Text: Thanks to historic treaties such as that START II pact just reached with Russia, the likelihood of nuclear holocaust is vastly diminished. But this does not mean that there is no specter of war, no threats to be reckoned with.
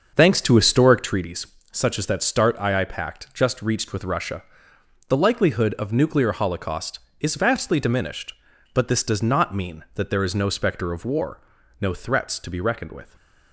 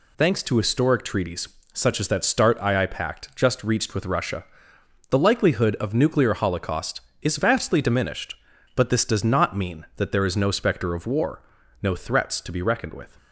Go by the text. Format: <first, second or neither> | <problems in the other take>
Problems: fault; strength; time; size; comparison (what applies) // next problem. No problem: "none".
second | starts louder than the rest; until 1.2 s; 6.5 dB // pauses between "treaties" and "such"; slight; at 1.4 s; 0.26 s long; slight in the second